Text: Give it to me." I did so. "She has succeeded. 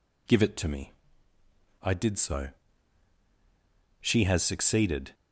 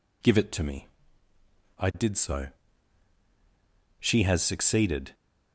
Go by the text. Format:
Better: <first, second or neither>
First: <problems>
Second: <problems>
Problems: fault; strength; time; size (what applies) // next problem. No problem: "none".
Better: neither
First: none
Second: none